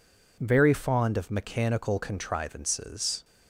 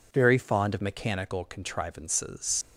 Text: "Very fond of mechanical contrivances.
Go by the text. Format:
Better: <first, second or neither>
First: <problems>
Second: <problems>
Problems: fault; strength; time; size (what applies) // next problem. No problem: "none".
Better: first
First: none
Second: leaves "contrivances" unfinished; at 2.6 s; 95 ms